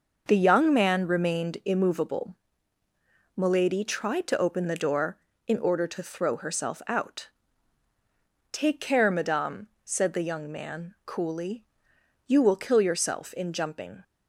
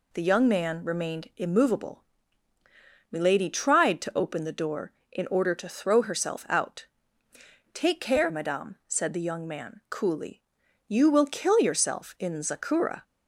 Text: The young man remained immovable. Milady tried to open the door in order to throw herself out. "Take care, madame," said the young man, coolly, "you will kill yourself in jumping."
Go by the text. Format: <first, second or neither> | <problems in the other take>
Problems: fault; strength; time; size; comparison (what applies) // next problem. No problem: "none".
first | says "zakura" for "jumping"; at 12.4 s